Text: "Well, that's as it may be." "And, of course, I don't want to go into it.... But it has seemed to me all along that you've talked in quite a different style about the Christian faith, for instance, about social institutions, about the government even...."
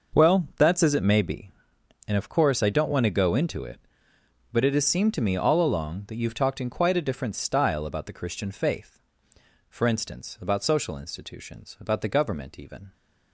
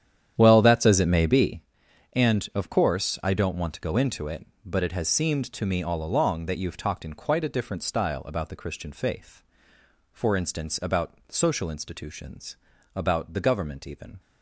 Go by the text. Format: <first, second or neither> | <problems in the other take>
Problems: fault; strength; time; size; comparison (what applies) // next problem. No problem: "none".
first | starts louder than the rest; strong; until 1.7 s; 9.5 dB